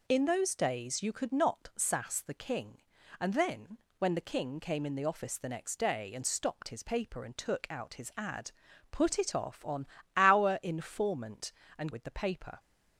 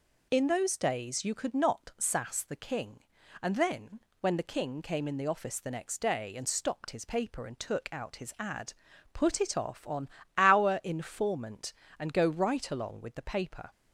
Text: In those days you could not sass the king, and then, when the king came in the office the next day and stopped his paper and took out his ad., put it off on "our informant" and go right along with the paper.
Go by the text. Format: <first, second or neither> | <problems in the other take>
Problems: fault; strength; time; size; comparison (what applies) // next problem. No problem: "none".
second | pauses between "on" and "our"; slight; at 9.8 s; 0.30 s long; slight in the second // skips "go right along"; at 11.9 s